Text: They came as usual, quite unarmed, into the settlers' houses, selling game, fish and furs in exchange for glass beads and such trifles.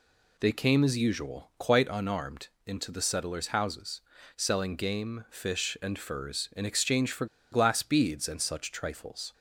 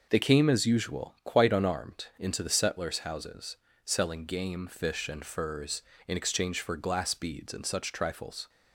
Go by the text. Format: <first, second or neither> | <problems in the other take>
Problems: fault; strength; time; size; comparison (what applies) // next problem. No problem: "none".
second | pauses between "for" and "glass"; slight; at 7.2 s; 0.26 s long